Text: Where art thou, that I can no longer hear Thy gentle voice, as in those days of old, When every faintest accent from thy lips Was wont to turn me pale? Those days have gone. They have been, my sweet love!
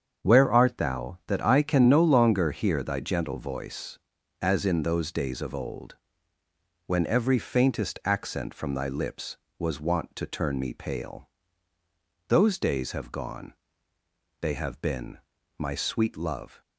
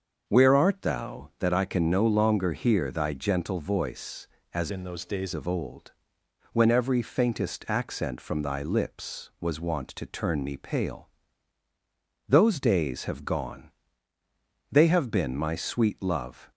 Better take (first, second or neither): first